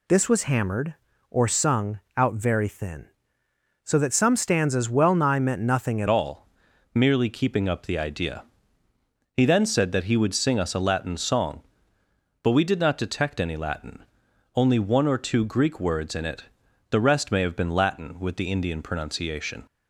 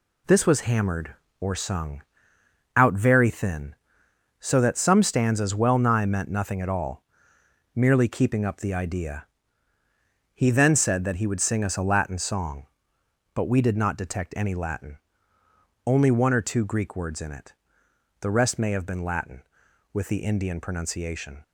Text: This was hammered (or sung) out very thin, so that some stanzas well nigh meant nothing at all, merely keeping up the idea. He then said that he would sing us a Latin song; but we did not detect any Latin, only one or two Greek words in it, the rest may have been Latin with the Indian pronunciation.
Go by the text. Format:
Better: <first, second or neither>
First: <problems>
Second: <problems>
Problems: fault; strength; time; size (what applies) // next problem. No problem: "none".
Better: second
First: changes voice at "all"; from 6.0 s on; 13.6 s long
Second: none